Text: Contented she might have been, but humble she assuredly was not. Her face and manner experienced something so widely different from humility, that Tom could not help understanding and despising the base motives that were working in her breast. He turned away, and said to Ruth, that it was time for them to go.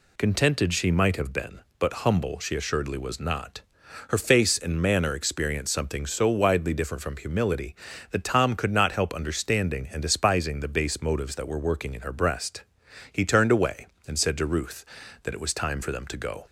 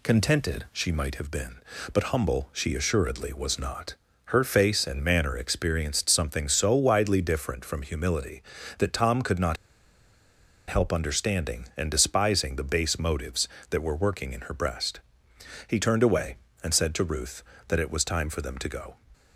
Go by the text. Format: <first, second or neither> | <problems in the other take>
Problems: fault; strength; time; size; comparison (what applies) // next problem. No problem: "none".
first | pauses between "not" and "help"; at 9.5 s; 1.1 s long